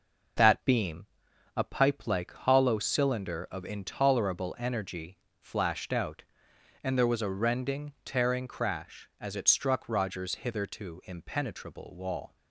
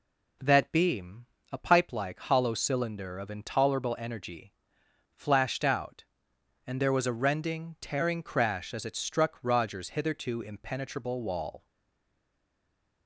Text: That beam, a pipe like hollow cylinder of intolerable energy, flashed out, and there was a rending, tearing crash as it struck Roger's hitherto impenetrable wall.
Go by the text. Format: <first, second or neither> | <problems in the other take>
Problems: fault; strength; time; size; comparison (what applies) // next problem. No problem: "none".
first | stays silent after the last word; noticeable; from 11.6 s on; 1.4 s long